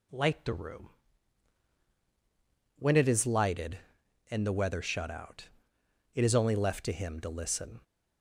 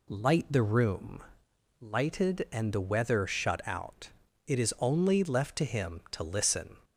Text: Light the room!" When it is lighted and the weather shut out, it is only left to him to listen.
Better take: first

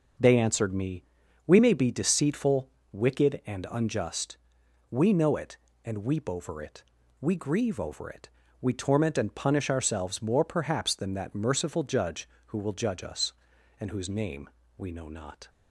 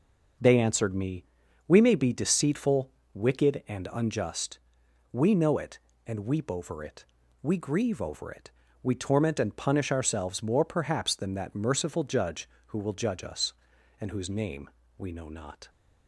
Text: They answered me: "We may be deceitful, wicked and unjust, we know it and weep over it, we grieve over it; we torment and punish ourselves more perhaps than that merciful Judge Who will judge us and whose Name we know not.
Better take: neither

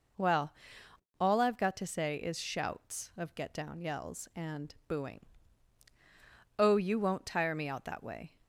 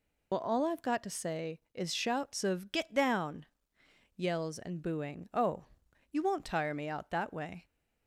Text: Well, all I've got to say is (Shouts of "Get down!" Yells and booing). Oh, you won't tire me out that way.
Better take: first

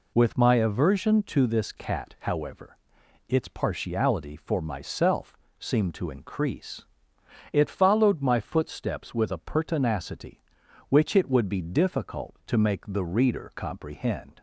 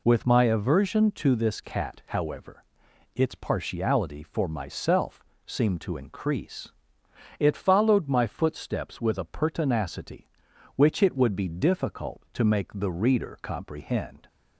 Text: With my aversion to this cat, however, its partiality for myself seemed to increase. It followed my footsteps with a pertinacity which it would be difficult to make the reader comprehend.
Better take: neither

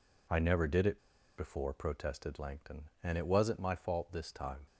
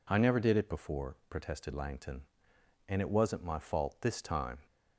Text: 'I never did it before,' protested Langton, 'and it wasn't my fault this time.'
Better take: second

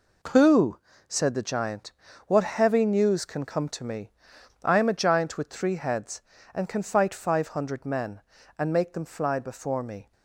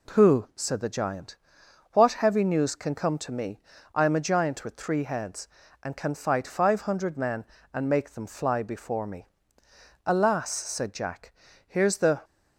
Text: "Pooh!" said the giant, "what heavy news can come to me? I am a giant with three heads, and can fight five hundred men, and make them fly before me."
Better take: first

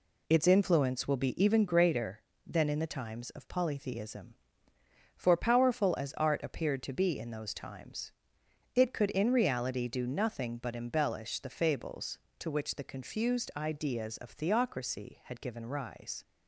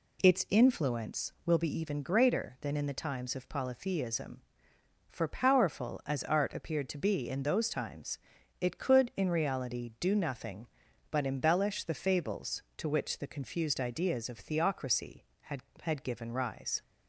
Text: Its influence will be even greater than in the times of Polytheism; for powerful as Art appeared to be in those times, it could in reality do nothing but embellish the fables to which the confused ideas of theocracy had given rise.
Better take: first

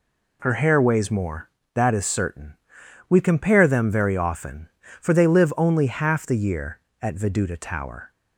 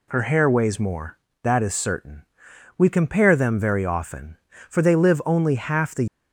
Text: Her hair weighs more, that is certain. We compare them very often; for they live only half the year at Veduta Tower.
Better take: first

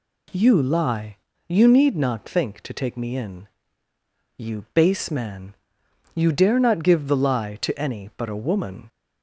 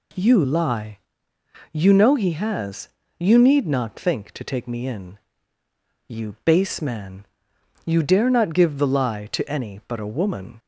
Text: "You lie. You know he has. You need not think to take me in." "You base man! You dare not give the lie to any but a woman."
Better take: second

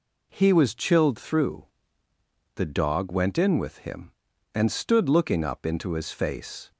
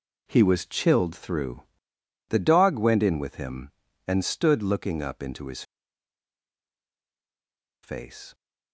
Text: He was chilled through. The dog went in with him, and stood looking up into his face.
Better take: first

